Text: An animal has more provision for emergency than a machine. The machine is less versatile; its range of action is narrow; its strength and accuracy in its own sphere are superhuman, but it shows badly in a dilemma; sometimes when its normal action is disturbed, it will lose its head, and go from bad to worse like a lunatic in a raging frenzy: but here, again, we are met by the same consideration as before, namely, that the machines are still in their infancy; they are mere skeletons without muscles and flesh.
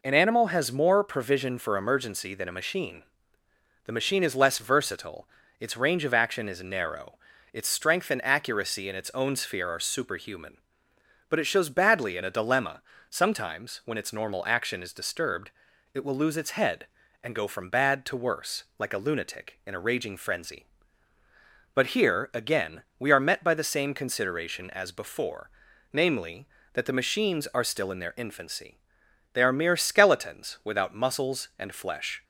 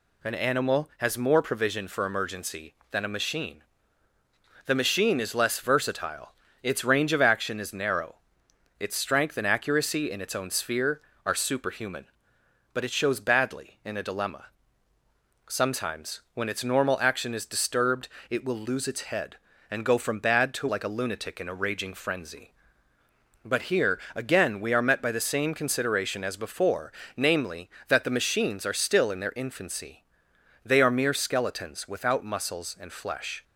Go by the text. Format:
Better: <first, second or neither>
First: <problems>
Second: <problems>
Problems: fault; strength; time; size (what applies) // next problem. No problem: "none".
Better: first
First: none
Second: skips "worse"; at 20.6 s